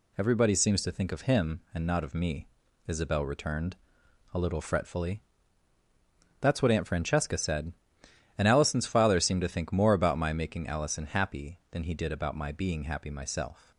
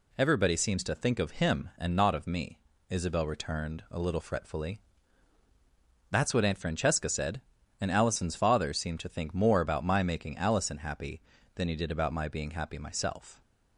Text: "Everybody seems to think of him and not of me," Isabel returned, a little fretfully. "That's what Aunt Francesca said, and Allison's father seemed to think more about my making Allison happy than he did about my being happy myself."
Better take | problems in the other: neither | none

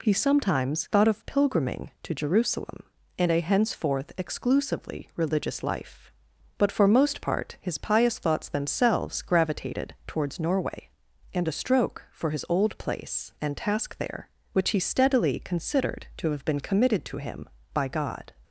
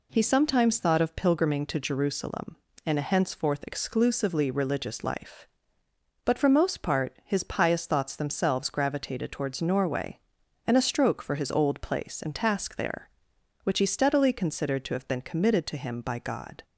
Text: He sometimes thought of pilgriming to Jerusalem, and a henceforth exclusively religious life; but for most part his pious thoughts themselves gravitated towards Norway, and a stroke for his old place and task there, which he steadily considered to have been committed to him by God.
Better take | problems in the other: neither | none

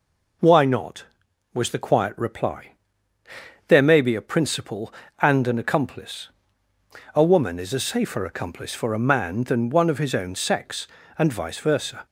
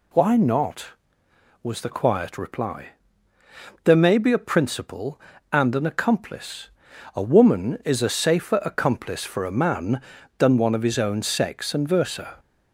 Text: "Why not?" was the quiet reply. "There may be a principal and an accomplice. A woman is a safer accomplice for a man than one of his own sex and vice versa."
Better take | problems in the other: first | skips "vice"; at 11.8 s

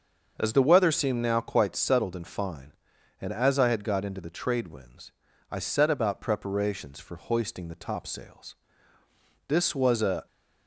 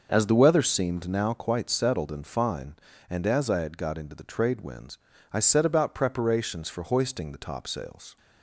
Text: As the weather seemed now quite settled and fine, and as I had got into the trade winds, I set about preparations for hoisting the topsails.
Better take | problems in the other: second | starts louder than the rest; until 1.3 s; 6.5 dB; noticeable in the second // goes on to say "This was a"; noticeable; from 9.4 s on; 0.78 s long

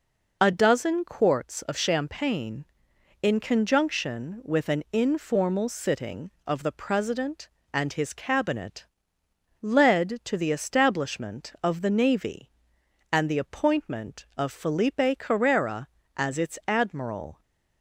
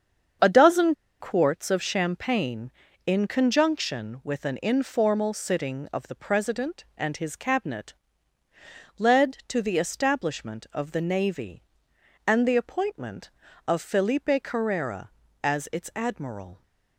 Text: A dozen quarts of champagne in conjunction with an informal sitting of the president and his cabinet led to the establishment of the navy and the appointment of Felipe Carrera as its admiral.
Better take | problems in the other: first | starts louder than the rest; strong; until 1.6 s; 7 dB // pauses between "dozen" and "quarts"; slight; at 0.9 s; 0.25 s long // pauses between "cabinet" and "led"; at 7.9 s; 1.0 s long; noticeable in the first

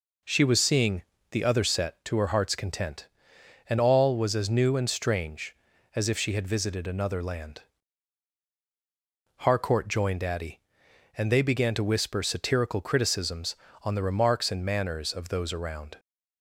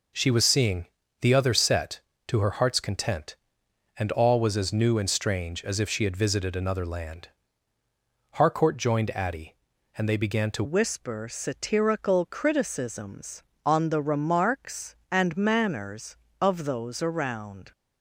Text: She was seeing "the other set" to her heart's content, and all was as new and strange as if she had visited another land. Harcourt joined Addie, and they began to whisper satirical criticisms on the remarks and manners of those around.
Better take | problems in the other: first | pauses between "seeing" and "the"; slight; at 0.8 s; 0.36 s long; slight in the first // changes voice at "whisper"; from 10.6 s on; 7.1 s long

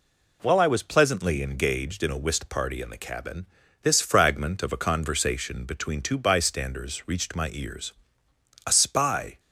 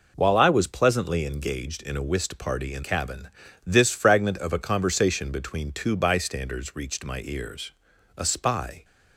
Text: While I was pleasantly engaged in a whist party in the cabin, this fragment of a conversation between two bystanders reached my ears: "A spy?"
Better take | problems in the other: first | skips "the"; at 2.8 s

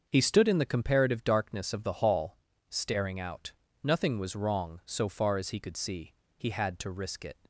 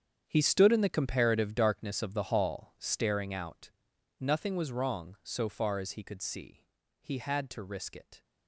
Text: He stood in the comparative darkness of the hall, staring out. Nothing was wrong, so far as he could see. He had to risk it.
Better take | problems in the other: first | gets quieter; strong; throughout; 15 dB // starts louder than the rest; strong; until 1.2 s; 8 dB; also in the first

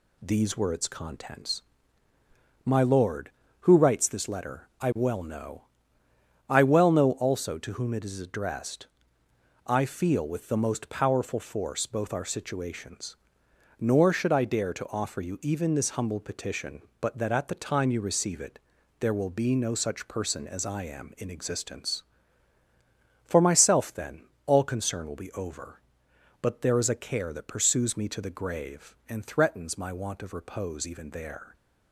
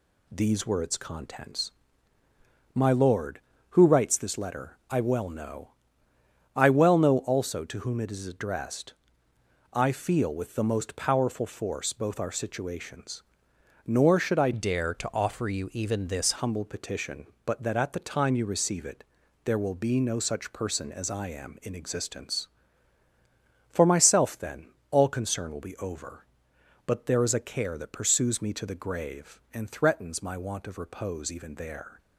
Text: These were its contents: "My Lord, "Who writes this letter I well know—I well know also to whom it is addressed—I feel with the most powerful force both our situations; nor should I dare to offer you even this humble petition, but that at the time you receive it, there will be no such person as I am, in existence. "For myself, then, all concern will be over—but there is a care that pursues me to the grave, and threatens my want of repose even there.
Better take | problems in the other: first | changes voice from "dare" to "this"; from 14.5 to 16.3 s; 1.8 s long

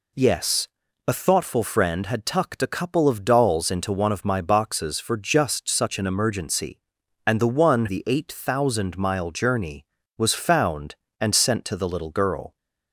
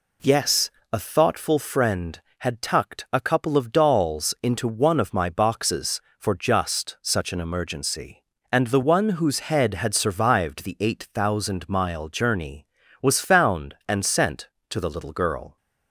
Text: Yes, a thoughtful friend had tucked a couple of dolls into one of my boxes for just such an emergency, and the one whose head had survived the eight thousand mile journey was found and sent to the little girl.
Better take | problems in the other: second | skips "whose head had survived"; at 7.8 s

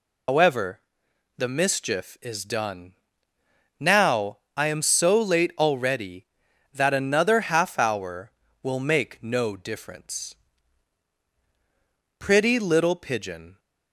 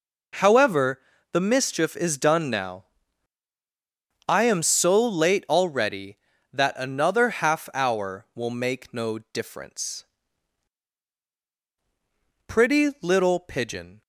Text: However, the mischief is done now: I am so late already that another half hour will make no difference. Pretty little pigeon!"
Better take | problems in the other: second | loses the start of "However"; at 0.2 s; 155 ms // pauses between "done" and "now"; noticeable; at 2.9 s; 0.86 s long

